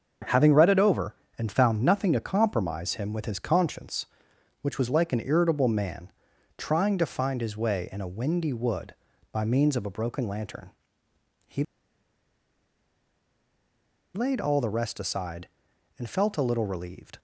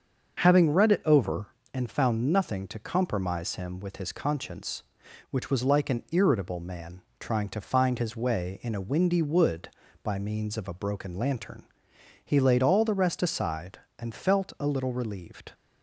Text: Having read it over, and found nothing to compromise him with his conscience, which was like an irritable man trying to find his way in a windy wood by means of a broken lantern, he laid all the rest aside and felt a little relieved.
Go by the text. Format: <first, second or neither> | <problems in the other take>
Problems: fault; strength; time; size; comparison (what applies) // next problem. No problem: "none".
second | starts louder than the rest; until 1.4 s; 6.5 dB; also in the second // pauses between "man" and "trying"; noticeable; at 6.1 s; 0.48 s long; slight in the second // pauses between "he" and "laid"; strong; at 11.6 s; 2.5 s long